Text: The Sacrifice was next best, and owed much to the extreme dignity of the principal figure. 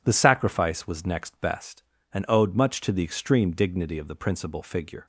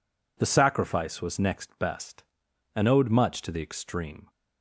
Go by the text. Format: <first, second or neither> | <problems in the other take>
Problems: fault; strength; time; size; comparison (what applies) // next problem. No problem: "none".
first | stops before "dignity of the principal figure"; at 4.2 s